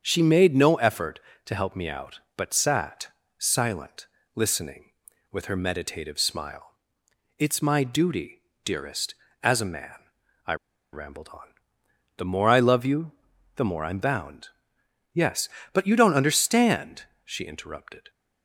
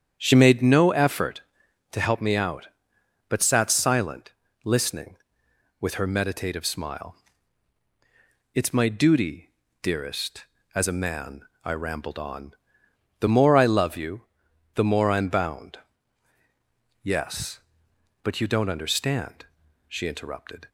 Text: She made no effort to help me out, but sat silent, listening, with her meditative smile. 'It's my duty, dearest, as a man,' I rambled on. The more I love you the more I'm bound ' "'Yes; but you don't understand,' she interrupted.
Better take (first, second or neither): second